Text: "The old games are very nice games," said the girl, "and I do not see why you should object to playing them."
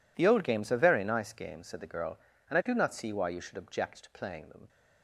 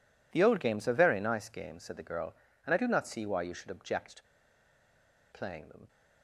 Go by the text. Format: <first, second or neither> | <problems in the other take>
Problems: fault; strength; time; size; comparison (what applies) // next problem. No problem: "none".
first | pauses between "to" and "playing"; at 4.2 s; 1.0 s long